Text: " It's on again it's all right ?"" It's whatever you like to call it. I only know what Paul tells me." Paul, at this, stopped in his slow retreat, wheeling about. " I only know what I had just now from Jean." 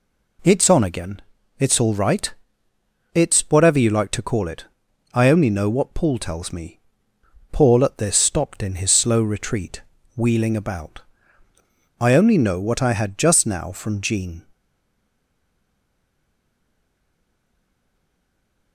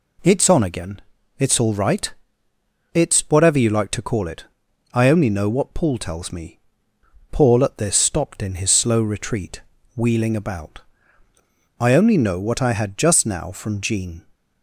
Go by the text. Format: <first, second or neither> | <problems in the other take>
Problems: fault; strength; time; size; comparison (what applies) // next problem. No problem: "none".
second | pauses between "again" and "it's"; at 1.2 s; 0.38 s long; also in the second // stays silent after the last word; strong; from 14.5 s on; 4.2 s long